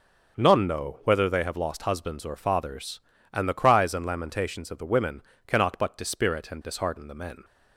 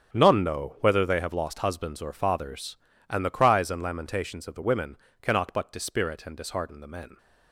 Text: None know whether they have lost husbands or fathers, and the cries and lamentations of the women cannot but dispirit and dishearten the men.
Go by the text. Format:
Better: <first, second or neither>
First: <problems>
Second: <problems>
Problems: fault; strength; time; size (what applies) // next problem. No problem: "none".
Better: first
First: starts louder than the rest; until 1.4 s; 6 dB // pauses between "women" and "cannot"; slight; at 5.2 s; 0.26 s long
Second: gets quieter; strong; throughout; 12.5 dB // starts louder than the rest; strong; until 1.1 s; 8 dB // pauses between "women" and "cannot"; slight; at 4.9 s; 0.26 s long